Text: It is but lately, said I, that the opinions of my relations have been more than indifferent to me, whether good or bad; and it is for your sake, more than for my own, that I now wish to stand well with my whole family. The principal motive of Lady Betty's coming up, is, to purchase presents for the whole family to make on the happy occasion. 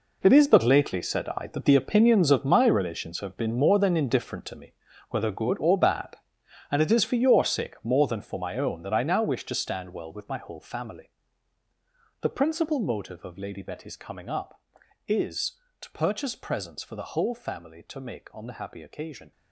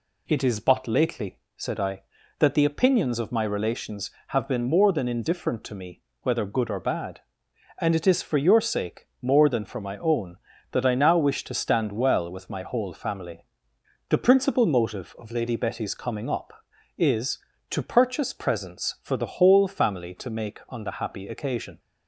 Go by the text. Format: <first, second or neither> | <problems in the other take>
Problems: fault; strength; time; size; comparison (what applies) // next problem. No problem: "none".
second | gets quieter; strong; throughout; 13 dB